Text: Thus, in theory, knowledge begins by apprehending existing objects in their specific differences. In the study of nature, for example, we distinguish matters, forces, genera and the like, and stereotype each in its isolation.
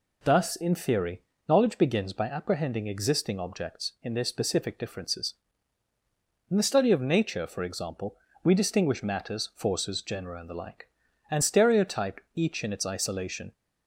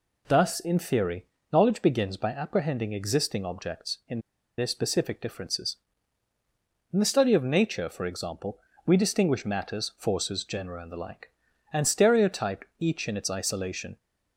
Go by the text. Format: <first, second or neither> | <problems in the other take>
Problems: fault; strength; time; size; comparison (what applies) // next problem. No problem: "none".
first | pauses between "in" and "their"; at 4.1 s; 0.38 s long